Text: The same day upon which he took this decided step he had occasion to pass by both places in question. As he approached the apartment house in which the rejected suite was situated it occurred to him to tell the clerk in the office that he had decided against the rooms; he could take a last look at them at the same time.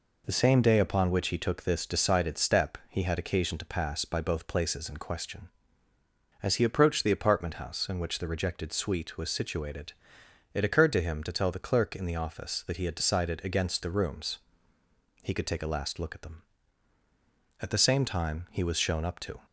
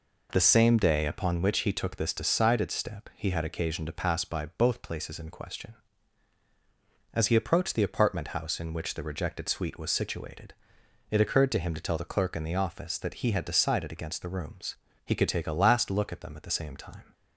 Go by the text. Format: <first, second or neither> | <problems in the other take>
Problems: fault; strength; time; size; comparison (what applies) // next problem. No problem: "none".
second | pauses between "situated" and "it"; noticeable; at 9.9 s; 0.62 s long; noticeable in the second // goes on to say "He was shown up to"; noticeable; from 18.4 s on; 0.96 s long